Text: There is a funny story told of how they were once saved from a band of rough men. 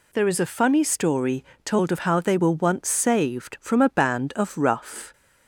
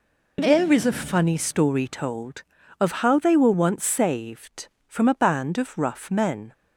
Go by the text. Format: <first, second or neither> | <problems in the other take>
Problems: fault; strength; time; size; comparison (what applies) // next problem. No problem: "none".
second | pauses between "story" and "told"; slight; at 1.4 s; 0.20 s long // stops before "men"; at 5.1 s